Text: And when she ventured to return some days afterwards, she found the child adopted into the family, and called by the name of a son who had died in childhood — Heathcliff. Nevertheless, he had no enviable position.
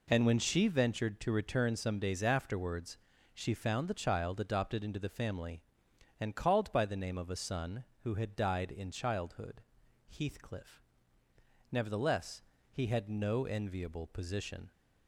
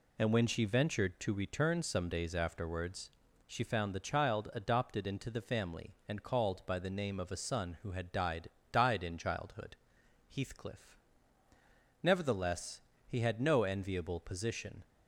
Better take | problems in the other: first | says "died" twice; at 8.7 s

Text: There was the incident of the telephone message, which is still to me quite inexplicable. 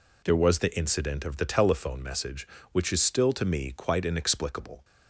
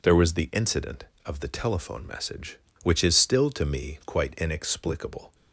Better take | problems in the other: neither | none

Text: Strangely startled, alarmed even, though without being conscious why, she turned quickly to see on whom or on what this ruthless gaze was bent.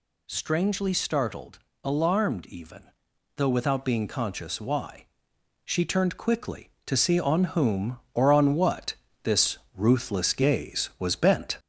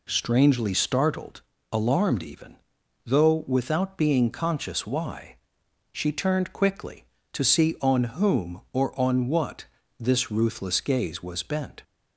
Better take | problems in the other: second | gets louder; slight; throughout; 3.5 dB // pauses between "what" and "this"; slight; at 8.9 s; 0.28 s long; slight in the second // pauses between "this" and "ruthless"; slight; at 9.5 s; 0.18 s long

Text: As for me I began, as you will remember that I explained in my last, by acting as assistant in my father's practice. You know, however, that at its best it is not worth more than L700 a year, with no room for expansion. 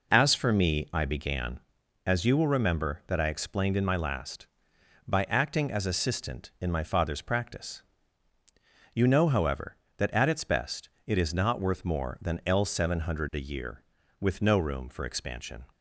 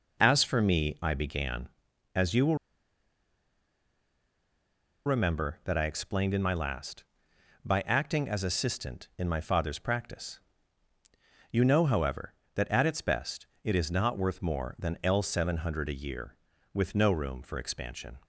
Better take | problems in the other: first | pauses between "will" and "remember"; strong; at 2.5 s; 2.4 s long // pauses between "best" and "it"; slight; at 13.4 s; 0.16 s long; slight in the first

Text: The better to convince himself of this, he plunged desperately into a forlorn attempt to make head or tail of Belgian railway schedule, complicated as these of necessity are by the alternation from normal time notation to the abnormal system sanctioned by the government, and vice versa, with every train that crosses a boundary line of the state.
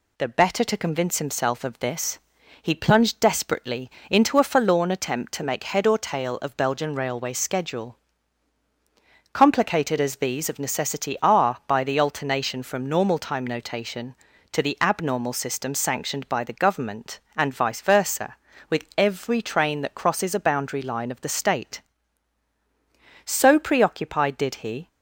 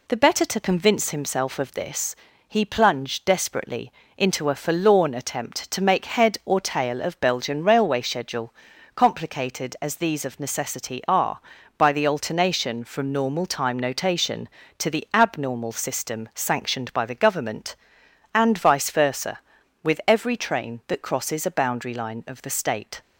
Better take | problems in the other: second | pauses between "desperately" and "into"; slight; at 3.8 s; 0.20 s long; slight in the second // goes on to say "So preoccupied did he"; from 23.2 s on; 1.6 s long

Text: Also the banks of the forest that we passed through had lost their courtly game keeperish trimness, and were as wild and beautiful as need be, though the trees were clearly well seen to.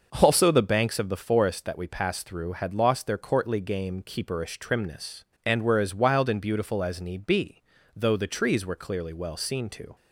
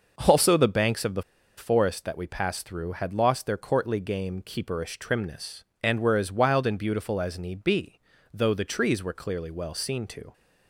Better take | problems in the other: first | pauses between "the" and "forest"; slight; at 1.2 s; 0.34 s long

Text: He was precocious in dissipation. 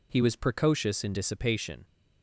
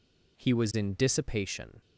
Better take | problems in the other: first | skips "precocious"; at 0.7 s

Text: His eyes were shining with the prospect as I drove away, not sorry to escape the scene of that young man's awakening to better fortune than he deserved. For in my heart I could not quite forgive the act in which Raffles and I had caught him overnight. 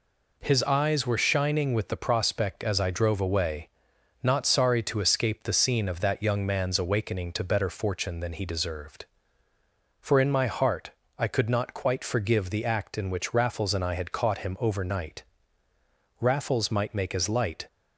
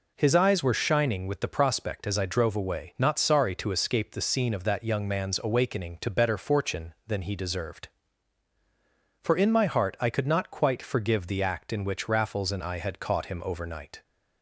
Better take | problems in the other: second | pauses between "heart" and "I"; slight; at 10.9 s; 0.28 s long // goes on to say "Raffles might make as light"; from 16.2 s on; 1.4 s long

